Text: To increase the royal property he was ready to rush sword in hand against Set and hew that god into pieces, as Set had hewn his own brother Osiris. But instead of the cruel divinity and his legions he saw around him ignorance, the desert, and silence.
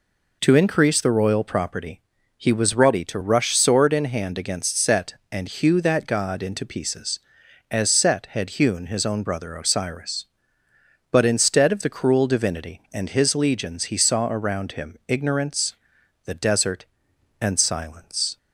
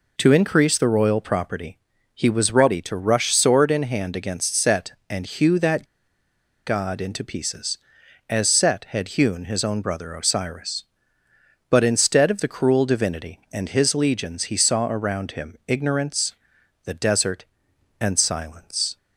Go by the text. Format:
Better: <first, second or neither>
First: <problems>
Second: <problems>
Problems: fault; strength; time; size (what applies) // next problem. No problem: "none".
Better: first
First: pauses between "property" and "he"; at 1.9 s; 0.38 s long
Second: pauses between "property" and "he"; at 1.7 s; 0.38 s long // pauses between "that" and "god"; noticeable; at 5.8 s; 0.82 s long